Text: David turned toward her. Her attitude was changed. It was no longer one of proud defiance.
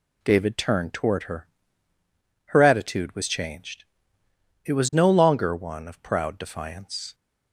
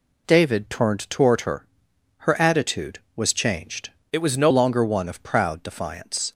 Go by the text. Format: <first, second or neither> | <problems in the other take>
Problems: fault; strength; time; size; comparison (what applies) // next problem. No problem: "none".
first | changes voice from "It" to "no"; from 4.1 to 4.5 s; 0.4 s long